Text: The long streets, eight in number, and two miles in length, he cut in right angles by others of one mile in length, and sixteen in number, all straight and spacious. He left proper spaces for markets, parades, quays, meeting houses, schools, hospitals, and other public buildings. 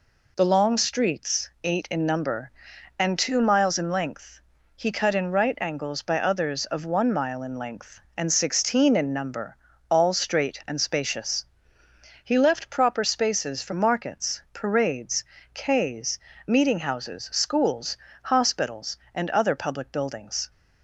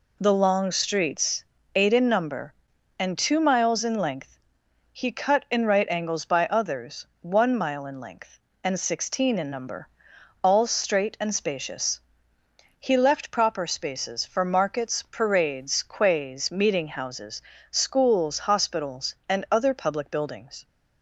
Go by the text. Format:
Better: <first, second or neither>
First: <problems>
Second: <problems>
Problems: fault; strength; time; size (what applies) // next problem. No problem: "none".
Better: first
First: none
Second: skips "of"; at 7.1 s